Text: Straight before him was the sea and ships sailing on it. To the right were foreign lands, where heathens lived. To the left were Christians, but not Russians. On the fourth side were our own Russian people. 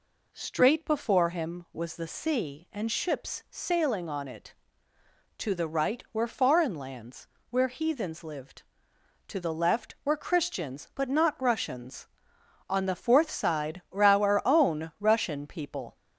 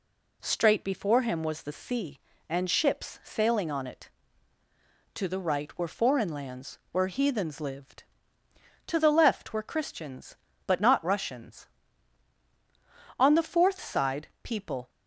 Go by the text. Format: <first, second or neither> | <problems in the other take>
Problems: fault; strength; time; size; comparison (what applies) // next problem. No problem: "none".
first | skips "were our own Russian"; at 14.3 s